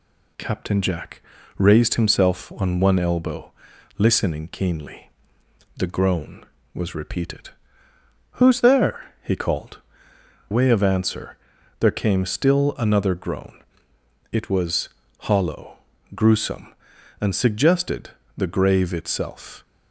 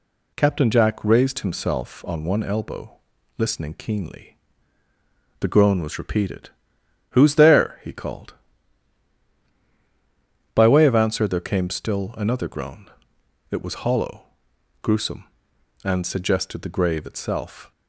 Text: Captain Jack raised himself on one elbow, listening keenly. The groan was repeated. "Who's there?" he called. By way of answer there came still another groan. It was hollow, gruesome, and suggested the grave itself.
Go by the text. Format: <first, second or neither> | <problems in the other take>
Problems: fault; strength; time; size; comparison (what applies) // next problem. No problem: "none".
second | pauses between "Jack" and "raised"; slight; at 1.2 s; 0.36 s long // skips "By"; at 10.1 s // pauses between "answer" and "there"; at 11.3 s; 0.44 s long // pauses between "was" and "hollow"; slight; at 14.8 s; 0.34 s long // pauses between "suggested" and "the"; slight; at 18.0 s; 0.28 s long